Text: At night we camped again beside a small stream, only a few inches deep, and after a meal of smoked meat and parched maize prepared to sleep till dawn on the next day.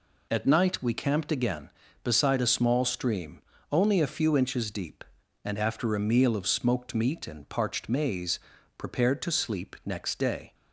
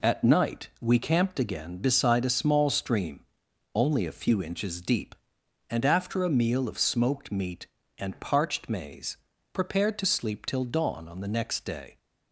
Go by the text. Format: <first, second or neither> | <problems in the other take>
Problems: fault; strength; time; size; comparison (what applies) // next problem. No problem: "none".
second | pauses between "maize" and "prepared"; at 8.3 s; 0.38 s long; slight in the second // skips "till dawn on the"; at 9.7 s